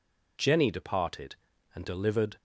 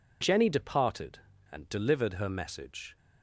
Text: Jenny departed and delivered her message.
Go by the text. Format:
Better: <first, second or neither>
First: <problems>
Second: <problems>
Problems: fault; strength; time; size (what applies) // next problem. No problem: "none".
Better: second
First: stops before "her message"; at 2.3 s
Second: none